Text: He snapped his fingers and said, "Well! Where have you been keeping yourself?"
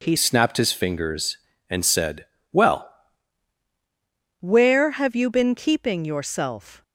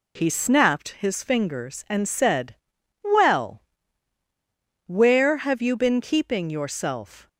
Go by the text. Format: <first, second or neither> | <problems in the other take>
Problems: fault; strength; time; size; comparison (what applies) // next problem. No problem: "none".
second | changes voice from "snapped" to "Well"; from 0.1 to 2.8 s; 2.7 s long